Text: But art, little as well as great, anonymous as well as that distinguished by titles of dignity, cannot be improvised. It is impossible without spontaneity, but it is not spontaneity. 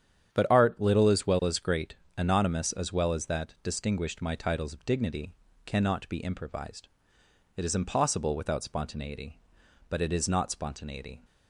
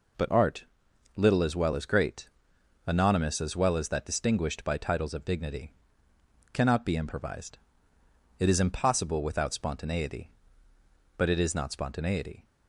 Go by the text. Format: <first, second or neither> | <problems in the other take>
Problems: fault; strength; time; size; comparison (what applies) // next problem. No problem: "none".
second | starts louder than the rest; strong; until 1.3 s; 9 dB // says "my" for "by"; at 4.2 s